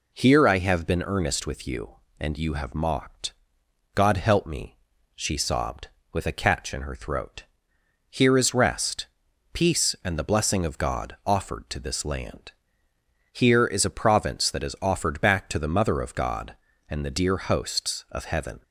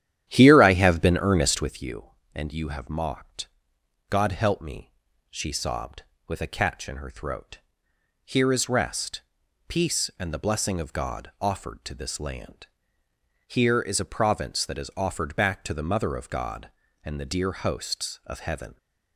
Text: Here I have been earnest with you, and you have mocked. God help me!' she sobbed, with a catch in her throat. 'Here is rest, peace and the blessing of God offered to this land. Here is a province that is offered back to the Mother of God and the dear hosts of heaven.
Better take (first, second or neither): first